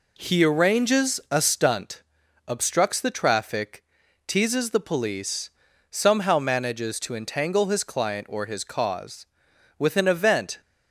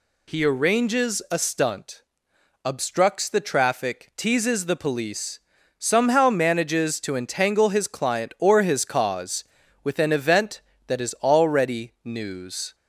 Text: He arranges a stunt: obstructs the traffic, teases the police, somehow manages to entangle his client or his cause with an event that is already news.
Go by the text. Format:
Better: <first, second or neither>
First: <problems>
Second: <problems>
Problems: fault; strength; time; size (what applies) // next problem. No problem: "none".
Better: second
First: stops before "that is already news"; at 10.6 s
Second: none